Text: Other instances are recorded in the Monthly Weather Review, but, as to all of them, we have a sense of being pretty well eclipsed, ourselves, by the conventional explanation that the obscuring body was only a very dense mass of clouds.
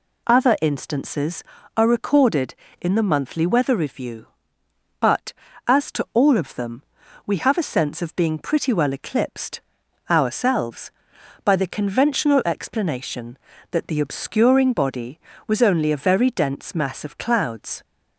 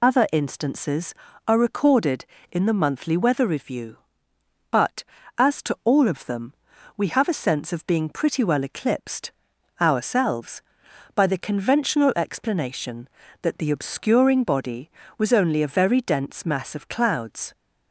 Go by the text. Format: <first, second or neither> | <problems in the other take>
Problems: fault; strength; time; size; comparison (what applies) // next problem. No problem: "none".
first | loses the start of "Other"; at 0.0 s; 60 ms